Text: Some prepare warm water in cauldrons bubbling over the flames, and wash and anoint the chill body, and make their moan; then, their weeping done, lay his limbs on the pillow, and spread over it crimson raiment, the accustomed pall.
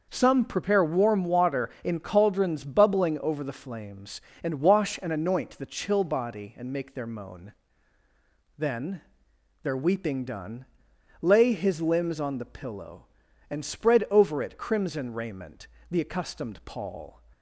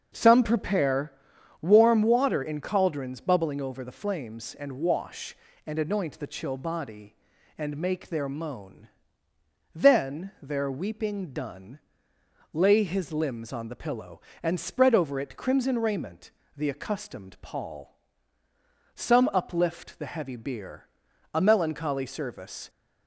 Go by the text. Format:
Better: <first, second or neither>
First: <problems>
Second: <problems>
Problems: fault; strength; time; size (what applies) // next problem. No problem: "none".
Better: first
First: none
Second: starts louder than the rest; until 1.6 s; 6.5 dB // pauses between "prepare" and "warm"; noticeable; at 1.1 s; 0.48 s long // goes on to say "Some uplift the heavy bier a melancholy service"; strong; from 18.9 s on; 3.7 s long